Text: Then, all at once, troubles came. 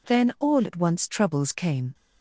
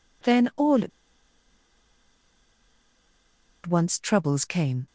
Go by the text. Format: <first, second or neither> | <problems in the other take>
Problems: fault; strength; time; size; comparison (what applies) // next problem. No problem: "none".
first | pauses between "at" and "once"; strong; at 0.9 s; 2.7 s long